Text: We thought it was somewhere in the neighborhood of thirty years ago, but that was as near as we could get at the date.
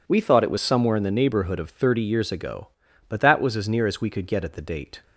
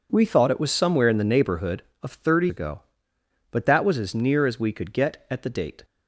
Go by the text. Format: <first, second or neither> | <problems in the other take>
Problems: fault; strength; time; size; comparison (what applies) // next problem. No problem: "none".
first | skips "years"; at 2.4 s